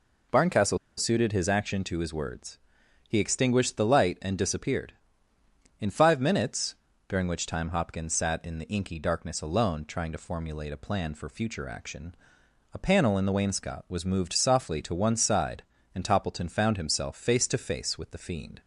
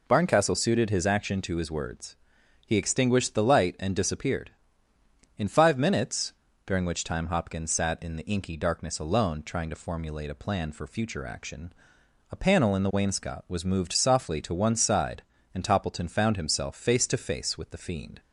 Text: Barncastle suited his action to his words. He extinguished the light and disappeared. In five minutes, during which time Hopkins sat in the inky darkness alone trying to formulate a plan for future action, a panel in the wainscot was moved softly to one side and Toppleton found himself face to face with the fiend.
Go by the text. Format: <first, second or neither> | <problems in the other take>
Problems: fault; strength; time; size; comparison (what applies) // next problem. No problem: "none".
second | pauses between "Barncastle" and "suited"; slight; at 0.7 s; 0.22 s long